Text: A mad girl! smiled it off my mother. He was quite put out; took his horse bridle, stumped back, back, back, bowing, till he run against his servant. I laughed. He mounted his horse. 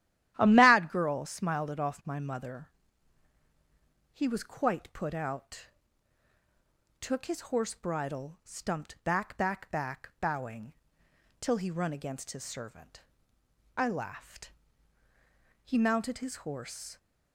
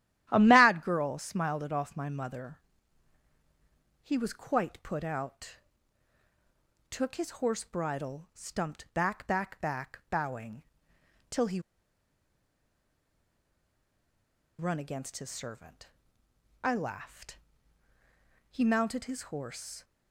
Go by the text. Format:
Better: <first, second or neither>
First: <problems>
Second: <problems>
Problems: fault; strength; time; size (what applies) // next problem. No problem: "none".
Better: first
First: starts louder than the rest; strong; until 1.3 s; 12.5 dB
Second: starts louder than the rest; strong; until 1.3 s; 12.5 dB // pauses between "he" and "run"; strong; at 11.5 s; 2.9 s long